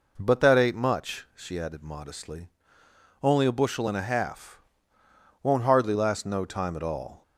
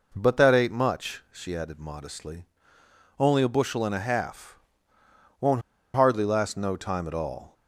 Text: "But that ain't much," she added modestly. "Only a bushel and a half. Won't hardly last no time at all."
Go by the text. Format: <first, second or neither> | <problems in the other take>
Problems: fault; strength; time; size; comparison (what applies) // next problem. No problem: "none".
first | pauses between "Won't" and "hardly"; slight; at 5.6 s; 0.33 s long